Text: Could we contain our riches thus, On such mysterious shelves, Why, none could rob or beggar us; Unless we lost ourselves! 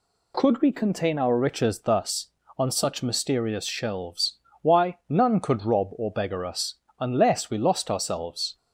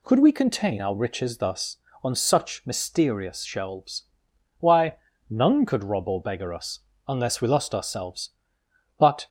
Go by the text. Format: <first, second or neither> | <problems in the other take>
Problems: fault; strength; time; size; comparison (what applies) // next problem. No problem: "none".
first | goes on to say "But"; slight; from 8.9 s on; 0.30 s long